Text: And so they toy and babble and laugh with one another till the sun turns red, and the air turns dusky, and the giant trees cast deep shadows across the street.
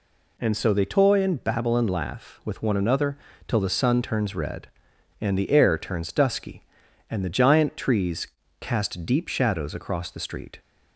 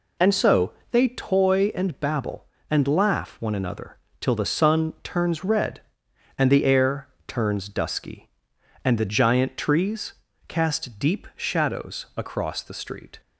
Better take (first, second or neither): first